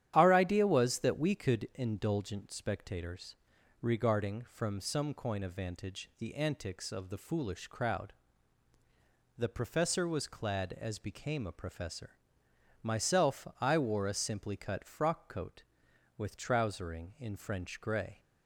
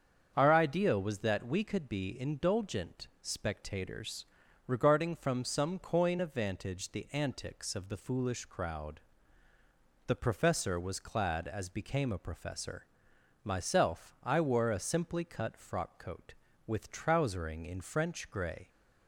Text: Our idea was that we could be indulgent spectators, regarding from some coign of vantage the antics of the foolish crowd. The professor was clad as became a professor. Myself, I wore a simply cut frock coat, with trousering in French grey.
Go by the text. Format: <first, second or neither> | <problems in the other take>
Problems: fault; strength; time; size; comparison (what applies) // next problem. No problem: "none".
second | starts louder than the rest; strong; until 1.1 s; 11 dB; strong in the second // skips "be"; at 1.7 s